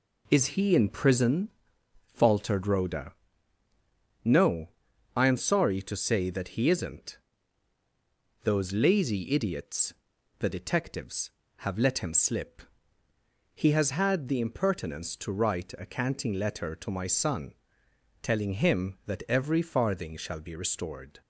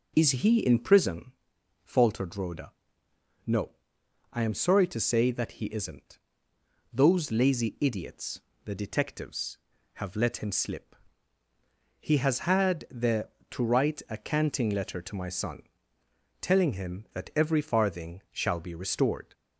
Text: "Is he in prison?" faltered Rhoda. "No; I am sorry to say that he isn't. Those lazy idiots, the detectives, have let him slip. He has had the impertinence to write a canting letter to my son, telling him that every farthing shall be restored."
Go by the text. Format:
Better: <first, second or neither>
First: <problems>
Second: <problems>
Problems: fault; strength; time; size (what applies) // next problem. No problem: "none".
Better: first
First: none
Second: skips "impertinence"; at 13.3 s